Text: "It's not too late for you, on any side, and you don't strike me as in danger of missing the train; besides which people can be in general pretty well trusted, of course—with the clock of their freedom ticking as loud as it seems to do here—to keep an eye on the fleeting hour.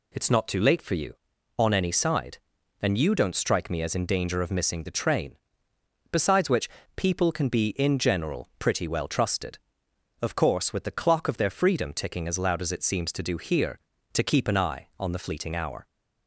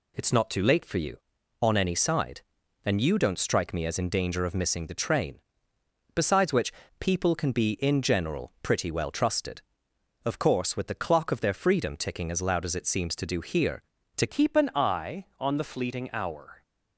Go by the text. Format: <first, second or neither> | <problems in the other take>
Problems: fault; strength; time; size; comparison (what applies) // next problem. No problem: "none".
first | pauses between "which" and "people"; slight; at 6.7 s; 0.28 s long; slight in the first // changes voice at "keep"; from 14.2 s on; 2.4 s long